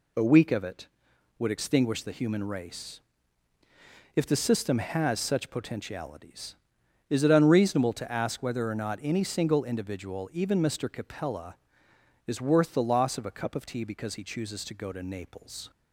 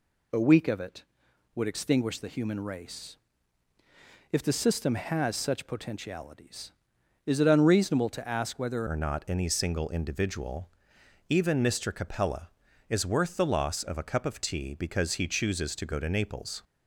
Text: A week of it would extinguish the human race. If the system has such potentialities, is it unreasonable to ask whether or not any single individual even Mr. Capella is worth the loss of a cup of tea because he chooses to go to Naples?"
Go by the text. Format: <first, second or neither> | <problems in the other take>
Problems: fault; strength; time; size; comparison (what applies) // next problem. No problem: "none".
first | changes voice at "or"; from 8.8 s on; 7.8 s long // pauses between "individual" and "even"; noticeable; at 10.6 s; 0.60 s long